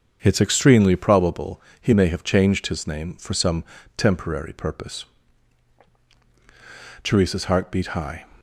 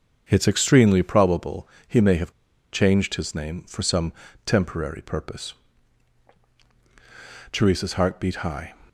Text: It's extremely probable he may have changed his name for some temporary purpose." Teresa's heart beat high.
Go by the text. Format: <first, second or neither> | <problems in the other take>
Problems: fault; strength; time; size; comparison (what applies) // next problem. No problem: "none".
first | starts louder than the rest; strong; until 1.3 s; 7 dB; strong in the first // pauses between "probable" and "he"; slight; at 1.6 s; 0.20 s long; slight in the first // pauses between "have" and "changed"; at 2.3 s; 0.40 s long // pauses between "some" and "temporary"; slight; at 4.1 s; 0.34 s long; slight in the first